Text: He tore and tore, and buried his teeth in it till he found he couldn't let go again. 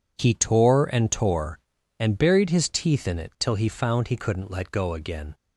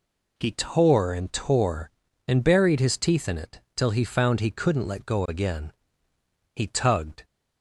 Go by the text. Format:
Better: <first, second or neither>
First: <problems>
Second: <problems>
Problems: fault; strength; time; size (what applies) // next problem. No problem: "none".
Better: first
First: none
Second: goes on to say "He tugged"; noticeable; from 6.5 s on; 0.70 s long